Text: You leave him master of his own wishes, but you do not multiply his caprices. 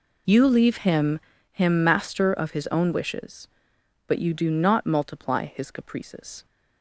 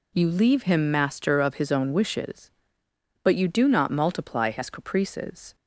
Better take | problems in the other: second | says "him" twice; at 1.5 s

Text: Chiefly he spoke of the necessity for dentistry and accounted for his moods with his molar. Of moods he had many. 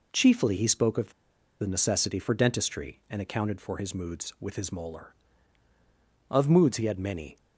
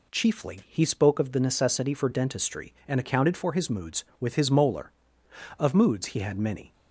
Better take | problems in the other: second | pauses between "of" and "the"; noticeable; at 1.1 s; 0.48 s long

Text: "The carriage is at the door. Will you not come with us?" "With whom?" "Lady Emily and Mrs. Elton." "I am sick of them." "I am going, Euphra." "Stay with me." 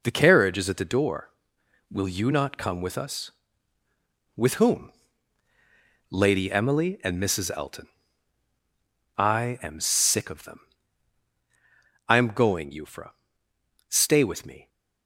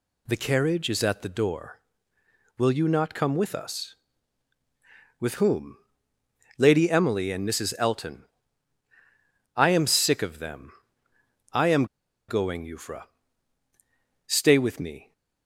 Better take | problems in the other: first | pauses between "am" and "going"; at 11.8 s; 0.43 s long

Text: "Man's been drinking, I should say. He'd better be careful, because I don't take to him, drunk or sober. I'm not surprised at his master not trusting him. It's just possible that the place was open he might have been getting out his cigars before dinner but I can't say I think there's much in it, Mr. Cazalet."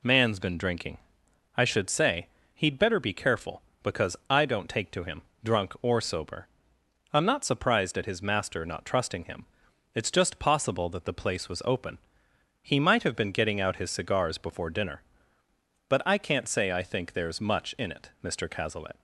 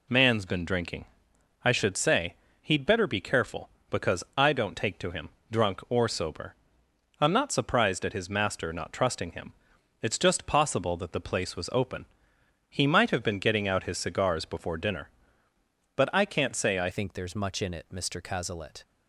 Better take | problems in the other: first | pauses between "open" and "he"; noticeable; at 12.0 s; 0.64 s long; noticeable in the first // changes voice at "think"; from 16.9 s on; 1.9 s long

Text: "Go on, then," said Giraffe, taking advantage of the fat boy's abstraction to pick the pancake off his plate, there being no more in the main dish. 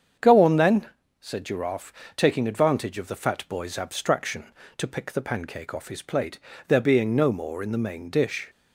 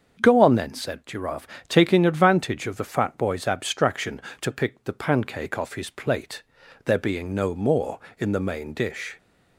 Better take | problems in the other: neither | starts louder than the rest; the same in both

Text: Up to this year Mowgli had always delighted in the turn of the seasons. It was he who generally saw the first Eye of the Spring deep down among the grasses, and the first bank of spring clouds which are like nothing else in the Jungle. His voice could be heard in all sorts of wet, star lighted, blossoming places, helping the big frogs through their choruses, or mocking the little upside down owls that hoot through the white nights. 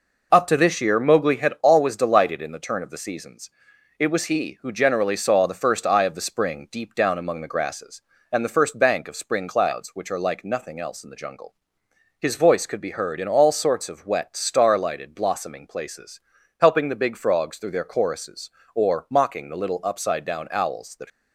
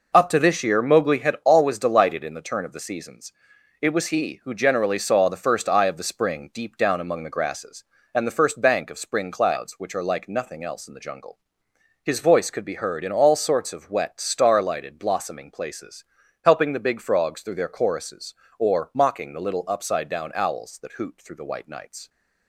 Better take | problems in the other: second | stops before "hoot through the white nights"; at 21.1 s

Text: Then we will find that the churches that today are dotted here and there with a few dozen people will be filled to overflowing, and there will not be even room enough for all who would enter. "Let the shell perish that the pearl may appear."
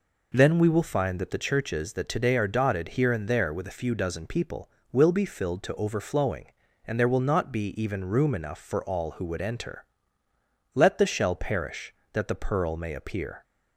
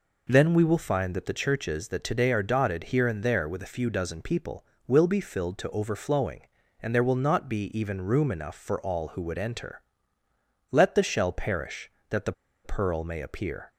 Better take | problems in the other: first | pauses between "the" and "pearl"; slight; at 12.3 s; 0.32 s long

